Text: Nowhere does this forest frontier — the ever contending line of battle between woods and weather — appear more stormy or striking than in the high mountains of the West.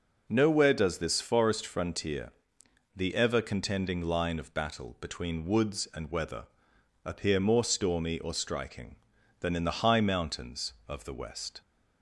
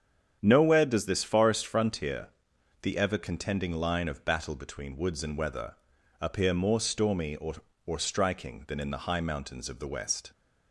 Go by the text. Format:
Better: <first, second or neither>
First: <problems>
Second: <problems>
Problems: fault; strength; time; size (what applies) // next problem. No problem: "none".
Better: first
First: none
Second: starts louder than the rest; strong; until 1.4 s; 8 dB // says "or" twice; at 7.8 s